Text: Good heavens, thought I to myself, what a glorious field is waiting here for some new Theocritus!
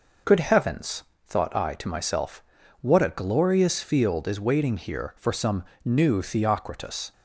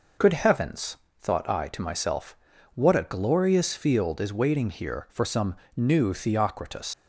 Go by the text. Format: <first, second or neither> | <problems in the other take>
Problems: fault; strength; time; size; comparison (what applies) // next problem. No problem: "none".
first | pauses between "some" and "new"; slight; at 5.5 s; 0.20 s long; slight in the first // leaves "Theocritus" unfinished; at 6.9 s; 95 ms